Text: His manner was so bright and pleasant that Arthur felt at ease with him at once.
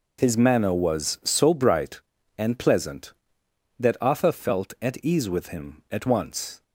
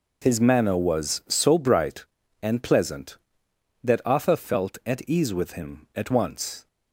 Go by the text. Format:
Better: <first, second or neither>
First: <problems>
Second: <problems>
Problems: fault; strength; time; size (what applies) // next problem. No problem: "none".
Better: neither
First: none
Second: none